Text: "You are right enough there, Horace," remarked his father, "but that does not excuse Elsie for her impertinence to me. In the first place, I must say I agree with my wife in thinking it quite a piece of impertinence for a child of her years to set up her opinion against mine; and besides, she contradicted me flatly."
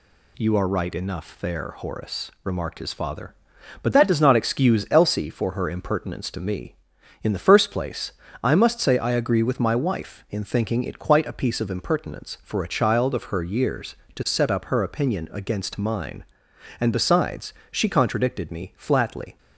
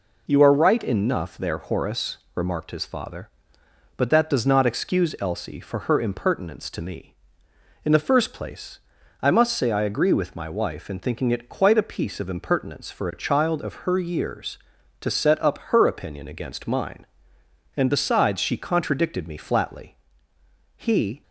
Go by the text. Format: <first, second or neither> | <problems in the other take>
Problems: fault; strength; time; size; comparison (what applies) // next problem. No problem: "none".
first | goes on to say "He"; slight; from 20.7 s on; 0.46 s long